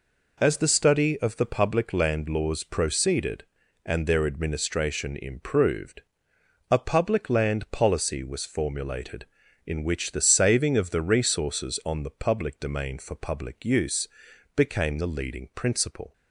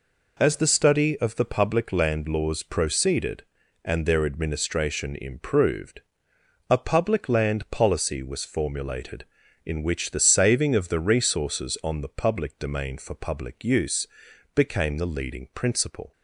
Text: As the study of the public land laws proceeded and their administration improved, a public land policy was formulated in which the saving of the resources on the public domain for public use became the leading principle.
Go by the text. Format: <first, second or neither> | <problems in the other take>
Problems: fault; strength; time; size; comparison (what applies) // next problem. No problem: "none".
neither | pauses between "use" and "became"; noticeable; the same in both